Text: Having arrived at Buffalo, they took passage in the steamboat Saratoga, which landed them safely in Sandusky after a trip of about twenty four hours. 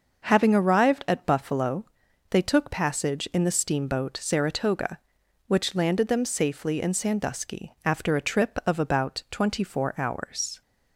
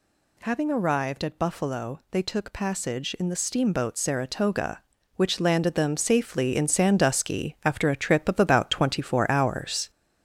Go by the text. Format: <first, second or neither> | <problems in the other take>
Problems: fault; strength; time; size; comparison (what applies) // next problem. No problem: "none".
first | gets louder; noticeable; throughout; 4.5 dB